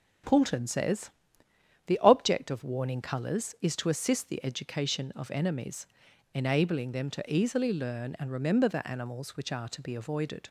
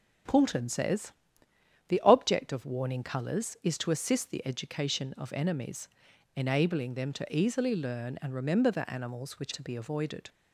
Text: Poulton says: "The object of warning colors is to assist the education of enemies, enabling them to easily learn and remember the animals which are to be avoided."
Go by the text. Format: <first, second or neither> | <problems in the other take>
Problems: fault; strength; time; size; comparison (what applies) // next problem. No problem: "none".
first | skips "are"; at 9.5 s